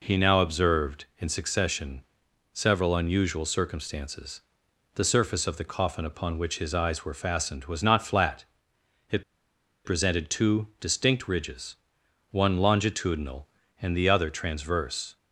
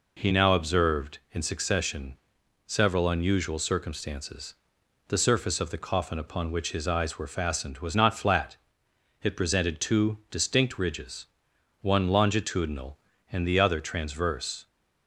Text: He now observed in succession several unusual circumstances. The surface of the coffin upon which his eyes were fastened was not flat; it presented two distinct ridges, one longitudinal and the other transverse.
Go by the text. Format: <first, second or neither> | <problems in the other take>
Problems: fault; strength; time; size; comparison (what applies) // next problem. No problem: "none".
second | pauses between "succession" and "several"; noticeable; at 2.0 s; 0.50 s long; noticeable in the second // pauses between "it" and "presented"; noticeable; at 9.2 s; 0.62 s long